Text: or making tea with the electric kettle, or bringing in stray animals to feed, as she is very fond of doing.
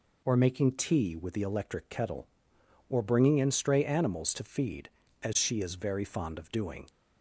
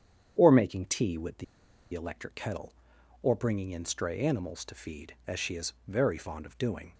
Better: first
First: none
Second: starts louder than the rest; strong; until 1.3 s; 9 dB // pauses between "the" and "electric"; noticeable; at 1.4 s; 0.48 s long // pauses between "is" and "very"; slight; at 5.7 s; 0.16 s long

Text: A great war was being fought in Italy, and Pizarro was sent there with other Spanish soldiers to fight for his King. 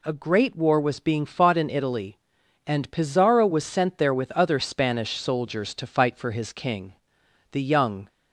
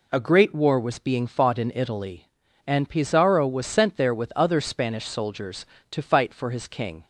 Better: second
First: goes on to say "The young"; from 7.5 s on; 0.56 s long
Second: none

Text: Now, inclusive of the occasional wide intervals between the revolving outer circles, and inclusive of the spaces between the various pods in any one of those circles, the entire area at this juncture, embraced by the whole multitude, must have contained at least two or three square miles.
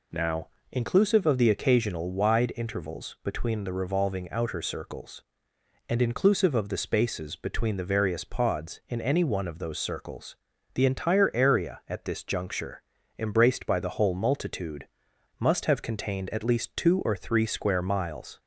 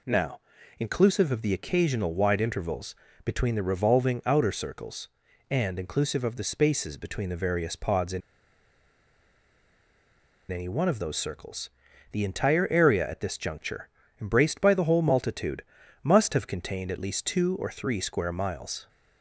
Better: first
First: none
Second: pauses between "intervals" and "between"; slight; at 2.9 s; 0.28 s long // pauses between "in" and "any"; strong; at 8.2 s; 2.3 s long

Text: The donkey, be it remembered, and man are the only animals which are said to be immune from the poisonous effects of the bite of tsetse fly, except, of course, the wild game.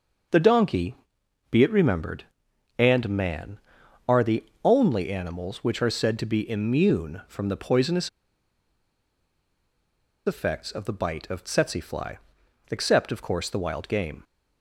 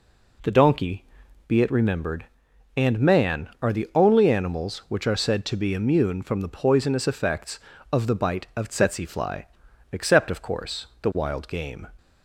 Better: second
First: starts louder than the rest; until 1.8 s; 6.5 dB // pauses between "the" and "only"; slight; at 4.4 s; 0.22 s long // pauses between "poisonous" and "effects"; strong; at 8.0 s; 2.1 s long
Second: none

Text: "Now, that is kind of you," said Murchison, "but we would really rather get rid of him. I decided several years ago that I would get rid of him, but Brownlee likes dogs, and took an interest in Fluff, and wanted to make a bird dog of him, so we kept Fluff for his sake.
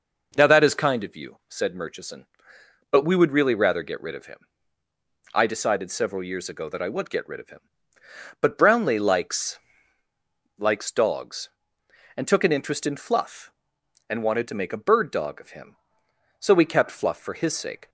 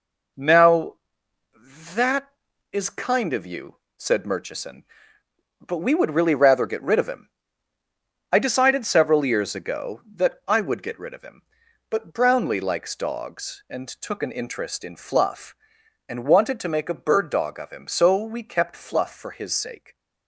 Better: second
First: says "likes" twice; at 10.5 s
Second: none

